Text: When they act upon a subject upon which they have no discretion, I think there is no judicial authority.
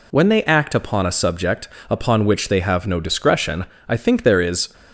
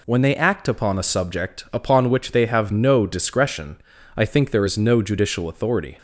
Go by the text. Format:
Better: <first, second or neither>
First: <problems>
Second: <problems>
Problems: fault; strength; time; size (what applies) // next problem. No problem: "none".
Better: second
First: pauses between "subject" and "upon"; slight; at 1.6 s; 0.20 s long // stops before "no judicial authority"; at 4.7 s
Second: none